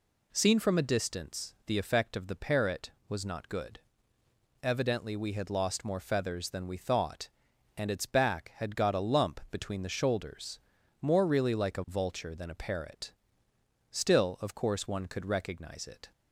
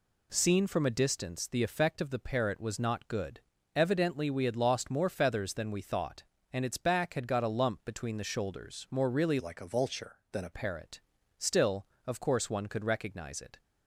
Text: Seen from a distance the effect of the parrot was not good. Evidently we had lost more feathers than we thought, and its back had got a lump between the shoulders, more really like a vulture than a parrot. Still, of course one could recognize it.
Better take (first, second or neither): first